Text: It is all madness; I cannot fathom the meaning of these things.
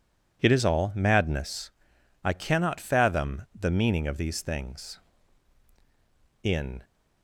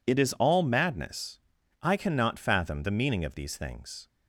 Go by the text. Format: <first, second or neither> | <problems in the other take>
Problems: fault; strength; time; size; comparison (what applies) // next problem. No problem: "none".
second | pauses between "fathom" and "the"; slight; at 3.4 s; 0.15 s long // goes on to say "In"; slight; from 6.4 s on; 0.40 s long